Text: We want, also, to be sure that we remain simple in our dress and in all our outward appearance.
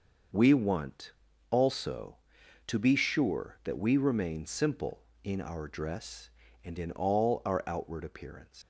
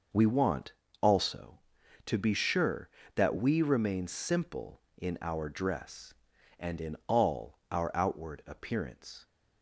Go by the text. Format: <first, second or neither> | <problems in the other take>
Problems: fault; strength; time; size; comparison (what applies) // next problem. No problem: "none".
second | starts louder than the rest; noticeable; until 1.7 s; 6 dB // leaves "appearance" unfinished; at 8.6 s; 190 ms